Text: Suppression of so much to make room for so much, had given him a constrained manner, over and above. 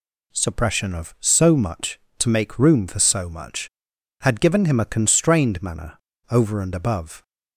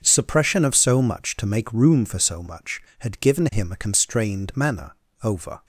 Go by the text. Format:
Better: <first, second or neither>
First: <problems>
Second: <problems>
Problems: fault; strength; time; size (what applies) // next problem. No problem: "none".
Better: first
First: none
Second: starts louder than the rest; until 1.0 s; 6.5 dB // stops before "and above"; at 5.6 s